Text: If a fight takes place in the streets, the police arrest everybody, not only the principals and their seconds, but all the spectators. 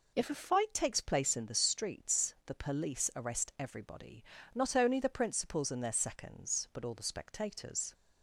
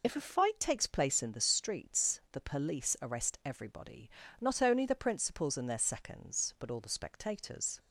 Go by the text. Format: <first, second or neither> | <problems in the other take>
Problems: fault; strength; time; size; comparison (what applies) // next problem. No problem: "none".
first | loses the start of "If"; at 0.0 s; 35 ms